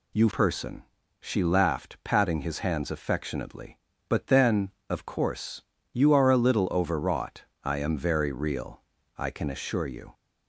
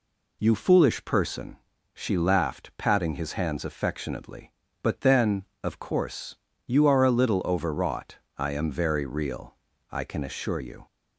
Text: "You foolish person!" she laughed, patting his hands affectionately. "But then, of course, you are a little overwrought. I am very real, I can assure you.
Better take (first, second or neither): second